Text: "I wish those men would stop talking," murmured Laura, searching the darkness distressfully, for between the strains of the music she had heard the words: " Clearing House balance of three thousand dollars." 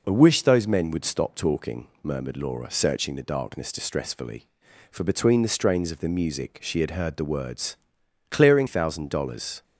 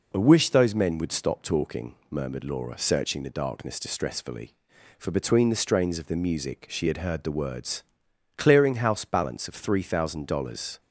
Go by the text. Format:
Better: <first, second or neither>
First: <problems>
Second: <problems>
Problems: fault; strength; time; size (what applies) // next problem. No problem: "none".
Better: second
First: skips "House balance of three"; at 8.6 s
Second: none